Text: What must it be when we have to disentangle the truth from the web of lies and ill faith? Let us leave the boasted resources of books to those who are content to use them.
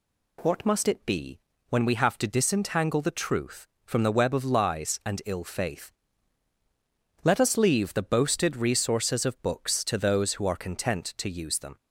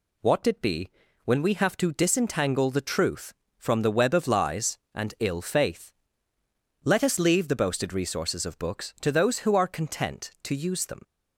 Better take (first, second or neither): first